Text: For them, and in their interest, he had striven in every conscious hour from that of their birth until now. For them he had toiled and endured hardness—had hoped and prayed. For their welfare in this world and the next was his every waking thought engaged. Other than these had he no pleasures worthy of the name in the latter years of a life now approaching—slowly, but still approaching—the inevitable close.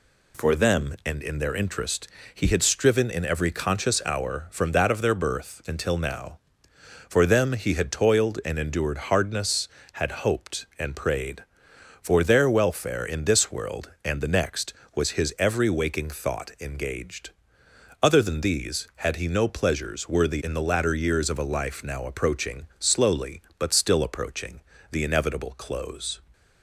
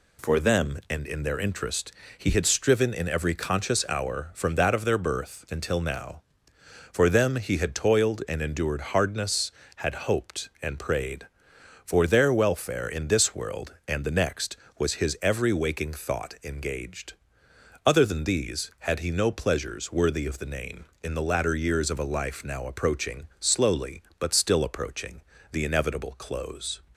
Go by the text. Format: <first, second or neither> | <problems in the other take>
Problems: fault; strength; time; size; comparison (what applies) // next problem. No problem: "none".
second | skips "of the name"; at 20.4 s